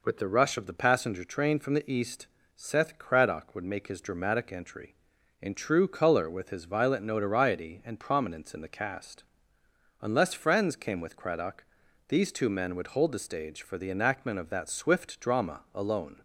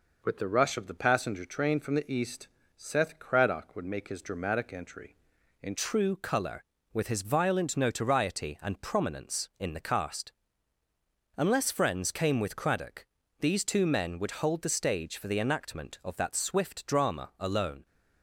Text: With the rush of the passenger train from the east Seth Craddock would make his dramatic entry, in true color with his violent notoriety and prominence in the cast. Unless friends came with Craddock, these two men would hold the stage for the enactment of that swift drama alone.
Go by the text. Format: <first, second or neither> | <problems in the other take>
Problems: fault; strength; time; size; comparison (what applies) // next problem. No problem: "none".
first | pauses between "east" and "Seth"; slight; at 2.4 s; 0.30 s long; slight in the first // changes voice at "true"; from 5.7 s on; 12.1 s long